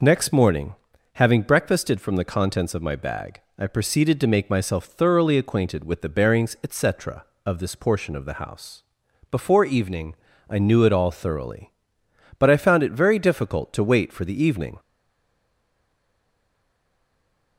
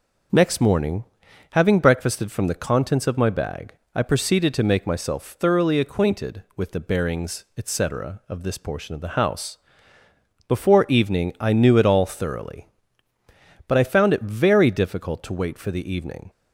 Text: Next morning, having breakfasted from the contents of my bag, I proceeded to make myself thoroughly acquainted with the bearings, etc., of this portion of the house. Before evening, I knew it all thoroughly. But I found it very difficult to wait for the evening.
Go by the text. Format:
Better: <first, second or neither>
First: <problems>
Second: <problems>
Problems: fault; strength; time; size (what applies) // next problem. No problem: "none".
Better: second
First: stays silent after the last word; strong; from 14.7 s on; 2.8 s long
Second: none